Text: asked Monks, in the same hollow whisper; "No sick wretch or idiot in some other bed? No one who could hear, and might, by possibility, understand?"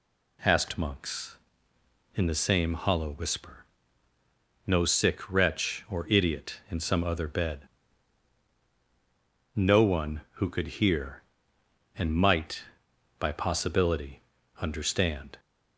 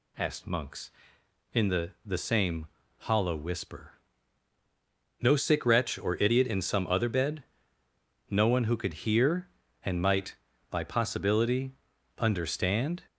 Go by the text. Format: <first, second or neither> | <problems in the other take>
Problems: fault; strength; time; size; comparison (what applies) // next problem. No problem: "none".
first | says "the" twice; at 2.0 s // pauses between "same" and "hollow"; slight; at 2.6 s; 0.30 s long